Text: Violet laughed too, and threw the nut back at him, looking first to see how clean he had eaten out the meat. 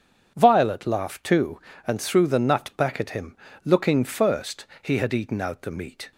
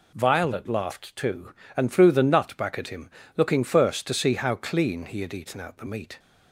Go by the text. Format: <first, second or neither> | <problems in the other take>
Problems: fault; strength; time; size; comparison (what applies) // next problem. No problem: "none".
second | skips "to see how clean"; at 4.7 s